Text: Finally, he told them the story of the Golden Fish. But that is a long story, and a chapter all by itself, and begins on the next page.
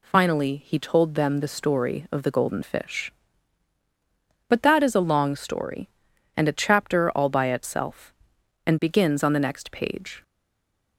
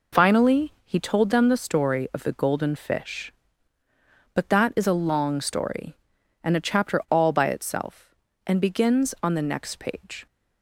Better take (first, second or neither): second